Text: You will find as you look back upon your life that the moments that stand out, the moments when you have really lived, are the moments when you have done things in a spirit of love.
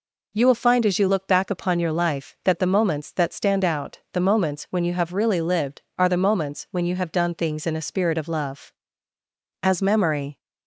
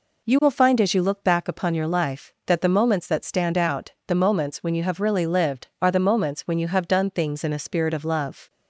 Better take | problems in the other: second | goes on to say "As memory"; noticeable; from 9.6 s on; 0.78 s long

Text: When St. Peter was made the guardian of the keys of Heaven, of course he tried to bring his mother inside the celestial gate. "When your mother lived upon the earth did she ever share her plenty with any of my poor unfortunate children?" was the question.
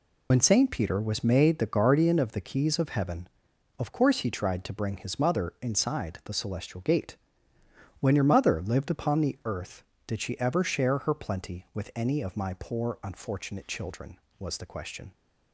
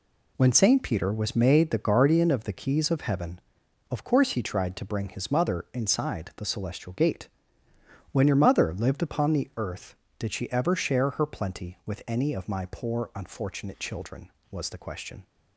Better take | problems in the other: second | loses the start of "When"; at 0.3 s; 50 ms

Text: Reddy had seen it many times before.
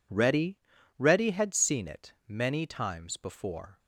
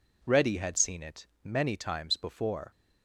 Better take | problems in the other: second | says "Reddy" twice; at 0.9 s // pauses between "it" and "many"; slight; at 2.1 s; 0.16 s long; slight in the second

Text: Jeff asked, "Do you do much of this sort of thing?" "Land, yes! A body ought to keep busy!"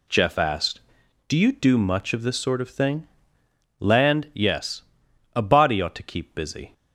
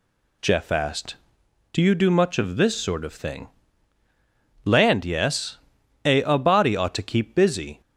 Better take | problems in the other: first | says "A" twice; at 6.2 s

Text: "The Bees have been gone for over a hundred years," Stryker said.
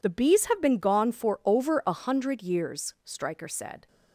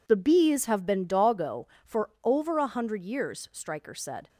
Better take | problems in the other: first | says "doggo" for "gone"; at 1.0 s

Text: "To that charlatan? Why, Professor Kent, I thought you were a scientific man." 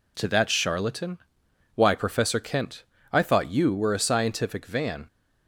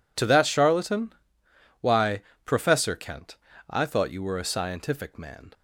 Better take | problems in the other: second | says "van" for "man"; at 4.6 s

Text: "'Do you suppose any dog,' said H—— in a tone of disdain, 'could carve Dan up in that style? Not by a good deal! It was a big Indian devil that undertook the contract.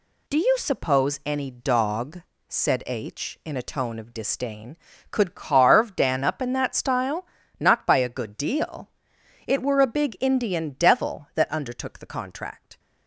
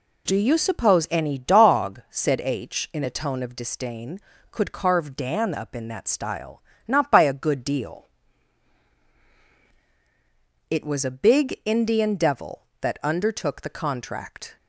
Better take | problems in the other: second | says "were" for "was"; at 9.6 s

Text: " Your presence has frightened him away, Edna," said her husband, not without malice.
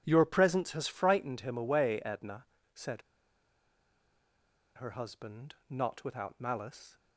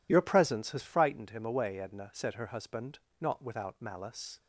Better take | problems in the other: second | pauses between "said" and "her"; strong; at 3.0 s; 1.7 s long

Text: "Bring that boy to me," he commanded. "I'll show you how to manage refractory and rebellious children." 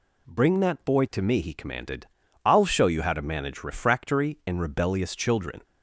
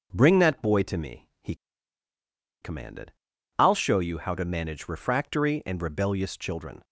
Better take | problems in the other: first | starts louder than the rest; until 1.1 s; 6.5 dB // pauses between "he" and "commanded"; at 1.5 s; 1.0 s long

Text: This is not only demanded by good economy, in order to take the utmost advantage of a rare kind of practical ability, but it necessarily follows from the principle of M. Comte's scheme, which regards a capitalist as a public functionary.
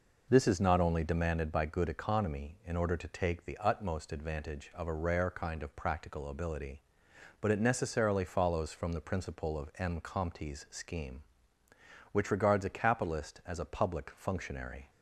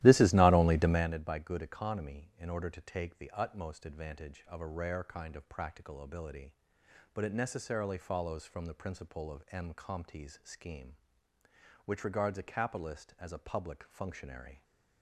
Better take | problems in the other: first | starts louder than the rest; strong; until 1.2 s; 15 dB

